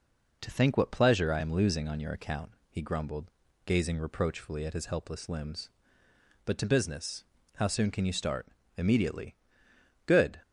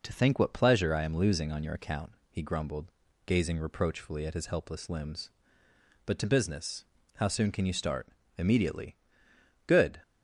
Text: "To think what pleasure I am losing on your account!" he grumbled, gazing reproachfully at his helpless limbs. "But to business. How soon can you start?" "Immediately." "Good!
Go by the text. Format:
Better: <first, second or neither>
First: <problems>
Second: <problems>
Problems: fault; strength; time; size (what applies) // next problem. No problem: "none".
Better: neither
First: none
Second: none